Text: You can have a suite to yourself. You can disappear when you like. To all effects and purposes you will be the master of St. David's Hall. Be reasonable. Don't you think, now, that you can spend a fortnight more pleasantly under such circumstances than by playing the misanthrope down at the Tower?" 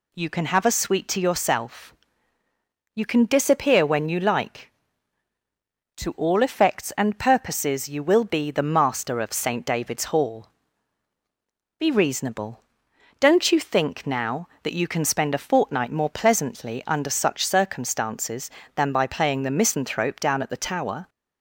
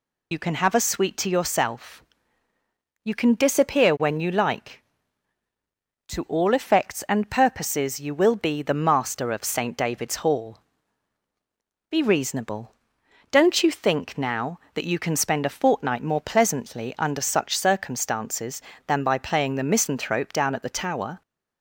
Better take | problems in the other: first | loses the start of "You"; at 0.3 s; 80 ms

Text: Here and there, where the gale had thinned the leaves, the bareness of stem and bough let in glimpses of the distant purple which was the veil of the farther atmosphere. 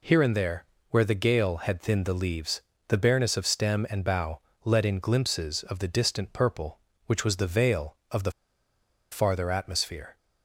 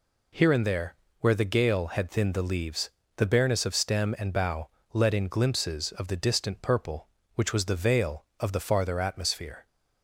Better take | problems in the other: second | pauses between "bough" and "let"; slight; at 4.4 s; 0.24 s long; slight in the second // pauses between "the" and "farther"; noticeable; at 8.3 s; 0.80 s long

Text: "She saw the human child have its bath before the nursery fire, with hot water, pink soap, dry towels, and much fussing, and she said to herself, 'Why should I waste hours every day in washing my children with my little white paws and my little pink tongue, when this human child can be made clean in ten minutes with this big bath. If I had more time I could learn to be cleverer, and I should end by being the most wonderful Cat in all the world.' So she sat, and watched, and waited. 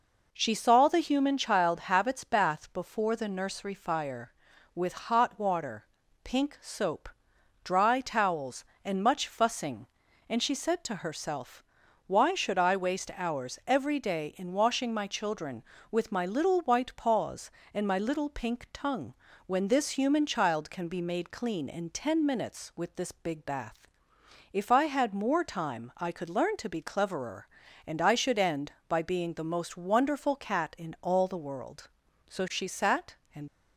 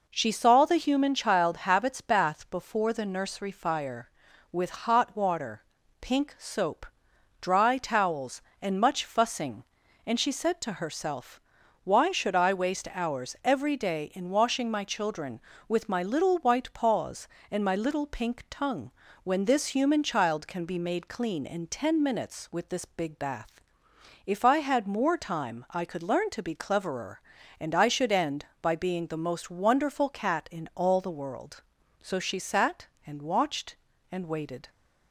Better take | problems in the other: second | stops before "watched and waited"; at 33.4 s

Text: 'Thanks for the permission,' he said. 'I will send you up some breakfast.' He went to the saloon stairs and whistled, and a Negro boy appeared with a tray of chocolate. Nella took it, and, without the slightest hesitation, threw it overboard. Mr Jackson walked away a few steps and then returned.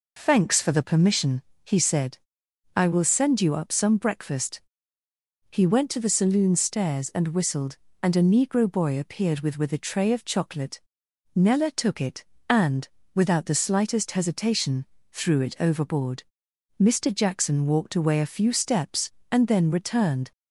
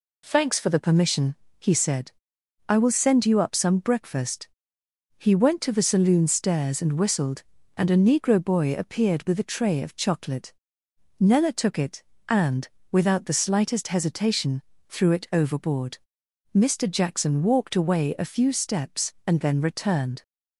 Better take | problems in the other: second | says "with" twice; at 9.5 s

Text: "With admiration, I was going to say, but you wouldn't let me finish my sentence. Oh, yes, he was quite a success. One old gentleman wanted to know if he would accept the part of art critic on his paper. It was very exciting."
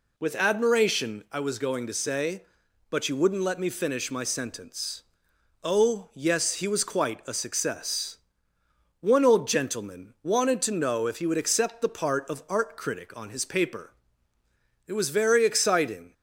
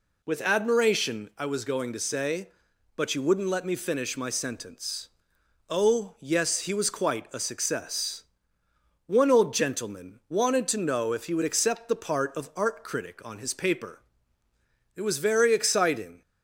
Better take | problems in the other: neither | none

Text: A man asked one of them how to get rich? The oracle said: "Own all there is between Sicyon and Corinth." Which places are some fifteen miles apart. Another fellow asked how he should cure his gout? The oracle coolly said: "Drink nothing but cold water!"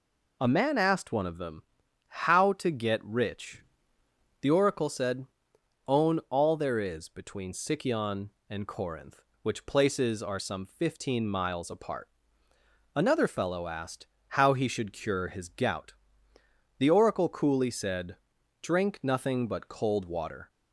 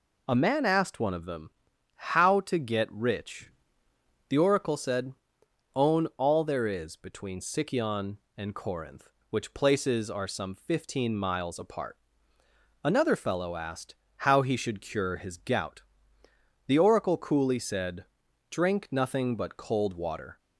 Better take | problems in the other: neither | pauses between "them" and "how"; noticeable; the same in both // pauses between "asked" and "how"; slight; the same in both

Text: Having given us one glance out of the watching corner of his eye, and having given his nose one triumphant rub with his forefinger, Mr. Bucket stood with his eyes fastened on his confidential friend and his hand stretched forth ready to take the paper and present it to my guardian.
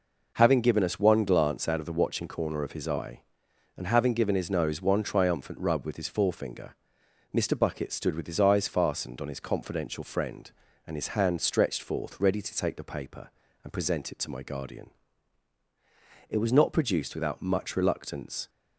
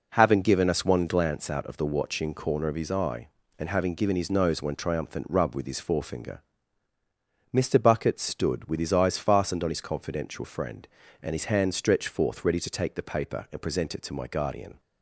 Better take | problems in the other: second | goes on to say "It was not produced without much reluctance"; strong; from 16.2 s on; 2.2 s long

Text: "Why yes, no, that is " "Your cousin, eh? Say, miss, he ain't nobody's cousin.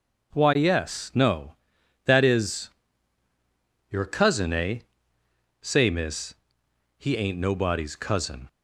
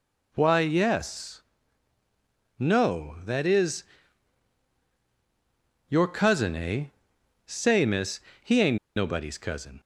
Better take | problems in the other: first | pauses between "ain't" and "nobody's"; slight; at 8.7 s; 0.18 s long

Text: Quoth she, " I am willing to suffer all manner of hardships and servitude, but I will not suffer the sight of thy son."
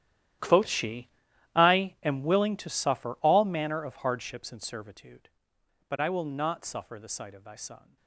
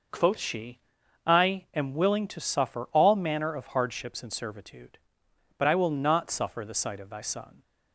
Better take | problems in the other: second | gets quieter; strong; throughout; 13.5 dB

